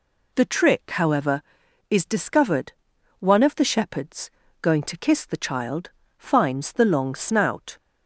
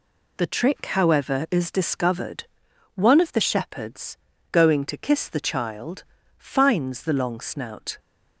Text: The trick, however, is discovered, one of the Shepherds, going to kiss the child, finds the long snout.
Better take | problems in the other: neither | none

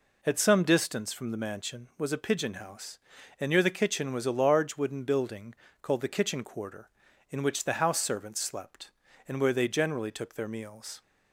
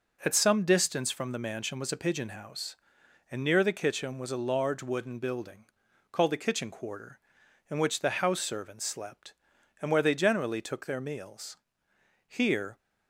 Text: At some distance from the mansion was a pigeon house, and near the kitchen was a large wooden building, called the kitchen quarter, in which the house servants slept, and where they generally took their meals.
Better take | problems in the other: first | goes on to say "Here"; from 12.2 s on; 0.52 s long

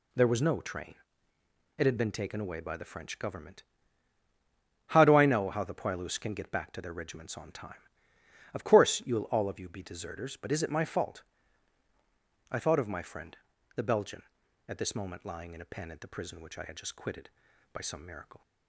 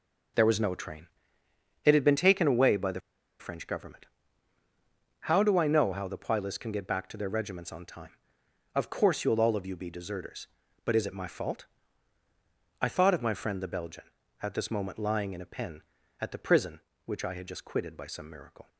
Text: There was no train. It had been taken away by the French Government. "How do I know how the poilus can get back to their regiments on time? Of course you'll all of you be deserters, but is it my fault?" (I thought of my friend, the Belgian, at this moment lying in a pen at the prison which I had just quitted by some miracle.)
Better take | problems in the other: first | pauses between "the" and "French"; at 2.9 s; 0.40 s long

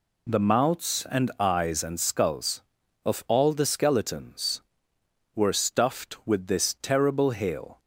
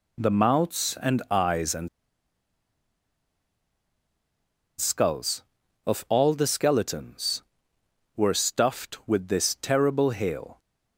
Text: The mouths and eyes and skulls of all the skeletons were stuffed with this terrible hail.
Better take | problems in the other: first | pauses between "and" and "skulls"; strong; at 1.8 s; 2.9 s long

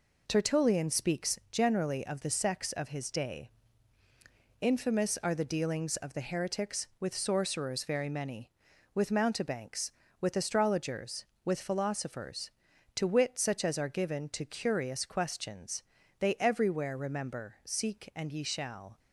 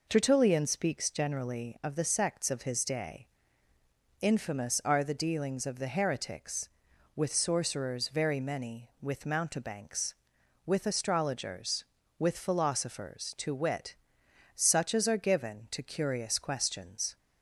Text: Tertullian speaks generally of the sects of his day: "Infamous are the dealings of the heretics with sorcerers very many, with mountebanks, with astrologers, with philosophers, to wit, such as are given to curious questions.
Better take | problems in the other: second | goes on to say "They everywhere remember Seek and ye shall"; strong; from 16.1 s on; 2.8 s long

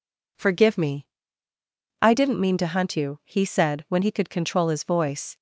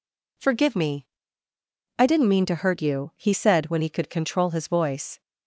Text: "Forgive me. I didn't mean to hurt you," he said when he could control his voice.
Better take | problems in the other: second | says "hunt" for "hurt"; at 2.6 s

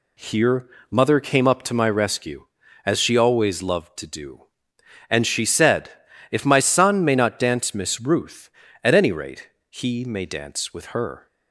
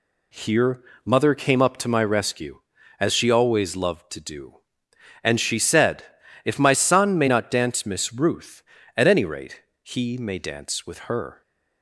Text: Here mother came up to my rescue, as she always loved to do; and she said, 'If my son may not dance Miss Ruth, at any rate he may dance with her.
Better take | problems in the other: neither | pauses between "Here" and "mother"; slight; the same in both // pauses between "rate" and "he"; slight; the same in both

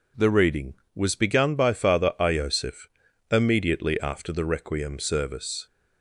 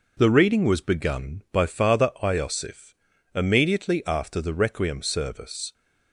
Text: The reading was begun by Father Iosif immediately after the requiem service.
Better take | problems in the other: neither | pauses between "Iosif" and "immediately"; the same in both

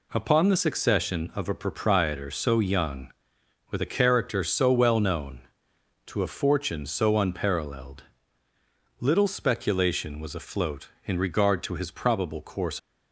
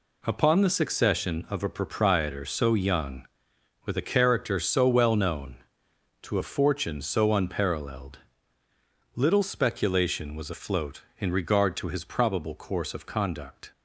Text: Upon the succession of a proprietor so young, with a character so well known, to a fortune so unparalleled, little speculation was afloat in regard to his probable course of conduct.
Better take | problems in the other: second | stops before "of conduct"; at 12.7 s

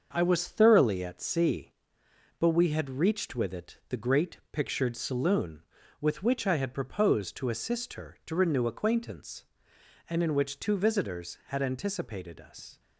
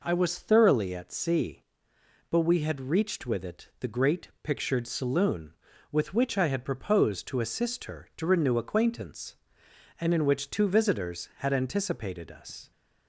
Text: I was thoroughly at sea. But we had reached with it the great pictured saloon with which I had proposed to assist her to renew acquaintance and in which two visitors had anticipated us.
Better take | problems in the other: second | gets quieter; noticeable; throughout; 6 dB

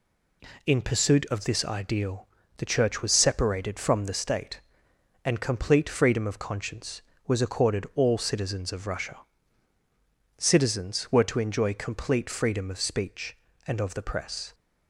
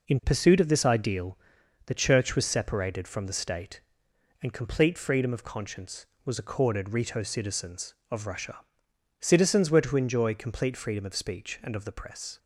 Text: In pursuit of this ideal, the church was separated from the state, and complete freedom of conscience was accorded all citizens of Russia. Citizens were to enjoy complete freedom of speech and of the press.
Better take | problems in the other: first | says "rito" for "all"; at 6.9 s

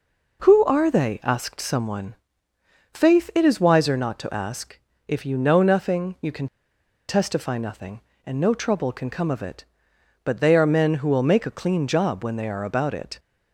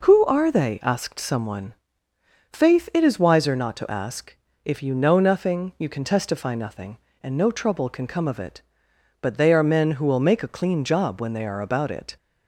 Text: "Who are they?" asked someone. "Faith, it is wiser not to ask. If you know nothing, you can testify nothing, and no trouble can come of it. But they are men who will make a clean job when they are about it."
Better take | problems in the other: second | pauses between "can" and "testify"; noticeable; at 6.4 s; 0.62 s long

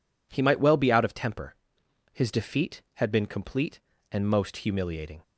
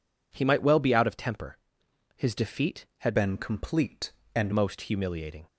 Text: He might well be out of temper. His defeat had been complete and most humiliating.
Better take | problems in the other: first | changes voice from "been" to "and"; from 3.1 to 4.5 s; 1.4 s long

